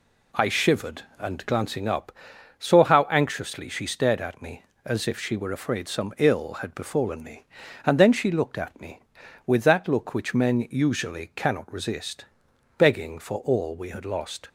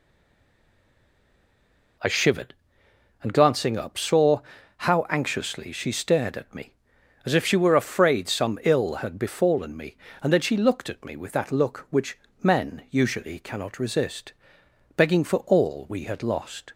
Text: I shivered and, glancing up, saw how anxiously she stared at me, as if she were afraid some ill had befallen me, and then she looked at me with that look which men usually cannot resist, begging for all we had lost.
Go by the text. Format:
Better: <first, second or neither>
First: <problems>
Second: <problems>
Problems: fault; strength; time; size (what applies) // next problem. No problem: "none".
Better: first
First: none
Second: stays silent before the first word; noticeable; until 1.9 s; 1.9 s long // pauses between "saw" and "how"; at 4.3 s; 0.38 s long // pauses between "which" and "men"; slight; at 12.1 s; 0.26 s long